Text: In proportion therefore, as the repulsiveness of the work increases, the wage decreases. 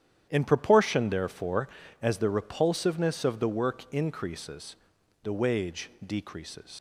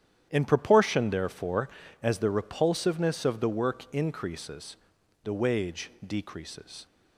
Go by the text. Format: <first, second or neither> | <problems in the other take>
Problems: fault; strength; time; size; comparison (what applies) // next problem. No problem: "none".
second | starts louder than the rest; strong; until 1.3 s; 10 dB; strong in the second // pauses between "wage" and "decreases"; slight; at 5.8 s; 0.16 s long; slight in the second // leaves "decreases" unfinished; at 6.7 s; 60 ms